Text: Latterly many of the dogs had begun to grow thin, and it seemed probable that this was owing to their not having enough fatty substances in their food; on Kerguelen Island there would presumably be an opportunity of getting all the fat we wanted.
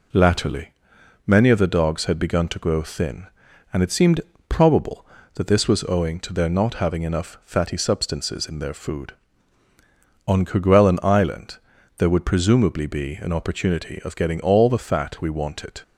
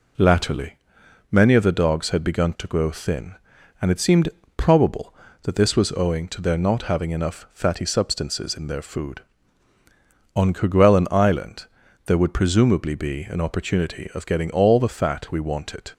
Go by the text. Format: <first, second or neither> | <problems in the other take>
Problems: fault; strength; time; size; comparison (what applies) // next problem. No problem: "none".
neither | pauses between "Latterly" and "many"; noticeable; the same in both // pauses between "seemed" and "probable"; slight; the same in both // pauses between "Island" and "there"; the same in both